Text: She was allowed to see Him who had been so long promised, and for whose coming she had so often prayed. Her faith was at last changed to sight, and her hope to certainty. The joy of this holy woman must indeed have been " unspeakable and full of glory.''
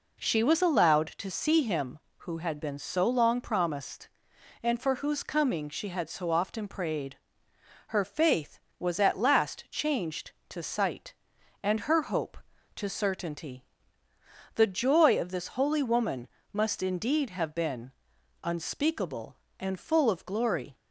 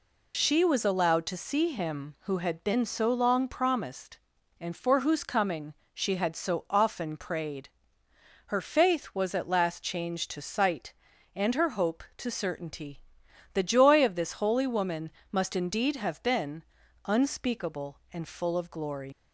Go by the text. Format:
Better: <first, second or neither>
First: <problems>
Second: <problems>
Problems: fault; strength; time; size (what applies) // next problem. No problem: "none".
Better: first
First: pauses between "woman" and "must"; slight; at 16.2 s; 0.24 s long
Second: pauses between "coming" and "she"; slight; at 5.7 s; 0.22 s long // pauses between "woman" and "must"; slight; at 15.0 s; 0.22 s long // leaves "glory" unfinished; at 19.1 s; 95 ms